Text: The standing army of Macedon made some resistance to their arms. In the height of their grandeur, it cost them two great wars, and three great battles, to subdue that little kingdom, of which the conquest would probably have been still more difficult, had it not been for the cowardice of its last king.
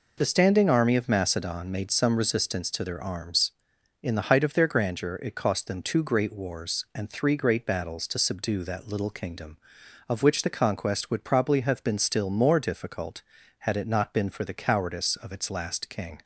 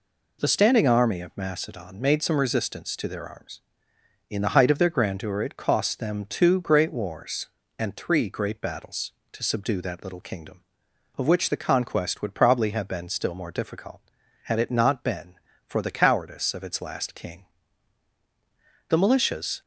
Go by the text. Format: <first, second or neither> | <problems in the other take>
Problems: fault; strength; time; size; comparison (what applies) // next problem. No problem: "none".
first | goes on to say "The militias"; noticeable; from 18.8 s on; 0.72 s long